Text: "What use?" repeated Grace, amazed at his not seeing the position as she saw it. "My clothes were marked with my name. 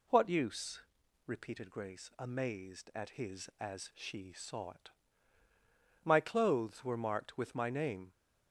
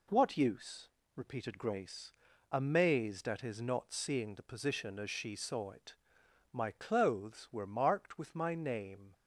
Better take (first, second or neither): second